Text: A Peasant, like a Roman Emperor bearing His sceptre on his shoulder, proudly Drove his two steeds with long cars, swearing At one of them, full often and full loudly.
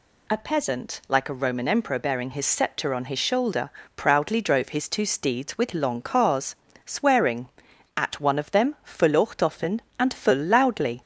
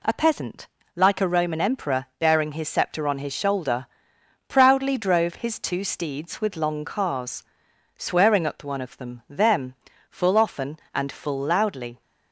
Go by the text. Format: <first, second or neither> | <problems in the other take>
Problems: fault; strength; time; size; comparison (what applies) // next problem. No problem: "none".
first | says "them" twice; at 9.2 s